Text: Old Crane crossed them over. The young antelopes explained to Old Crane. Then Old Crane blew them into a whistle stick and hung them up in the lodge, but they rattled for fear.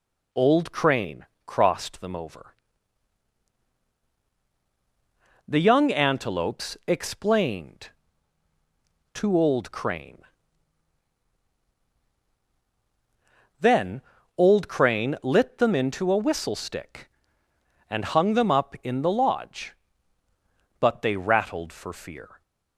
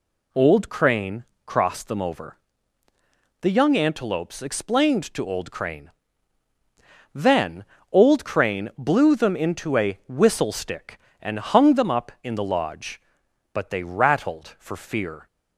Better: second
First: pauses between "Crane" and "crossed"; slight; at 1.2 s; 0.20 s long // pauses between "Then" and "Old"; slight; at 14.0 s; 0.36 s long // says "lit" for "blew"; at 15.2 s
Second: pauses between "Crane" and "crossed"; slight; at 1.2 s; 0.20 s long // pauses between "Then" and "Old"; slight; at 7.6 s; 0.26 s long

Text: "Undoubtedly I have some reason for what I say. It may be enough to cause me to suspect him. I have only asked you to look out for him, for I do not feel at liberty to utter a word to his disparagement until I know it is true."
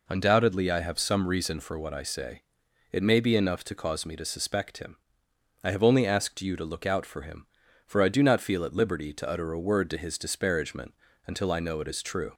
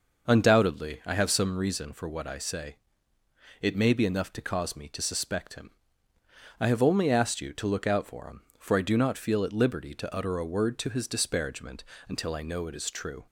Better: first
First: pauses between "disparagement" and "until"; slight; at 10.9 s; 0.32 s long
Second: starts louder than the rest; noticeable; until 1.5 s; 5.5 dB // pauses between "disparagement" and "until"; slight; at 11.8 s; 0.24 s long

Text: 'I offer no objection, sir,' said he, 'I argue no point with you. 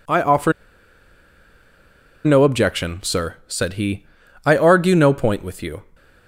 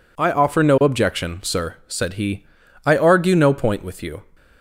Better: second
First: pauses between "offer" and "no"; strong; at 0.5 s; 1.7 s long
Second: none

